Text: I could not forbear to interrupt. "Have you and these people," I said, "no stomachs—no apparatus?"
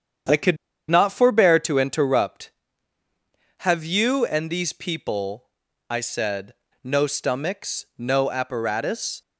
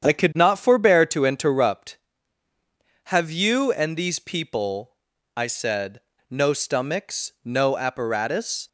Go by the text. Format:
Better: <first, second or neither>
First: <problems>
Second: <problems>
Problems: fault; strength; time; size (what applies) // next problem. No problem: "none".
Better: second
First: starts louder than the rest; strong; until 1.6 s; 8 dB // pauses between "could" and "not"; slight; at 0.5 s; 0.32 s long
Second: starts louder than the rest; strong; until 1.1 s; 8 dB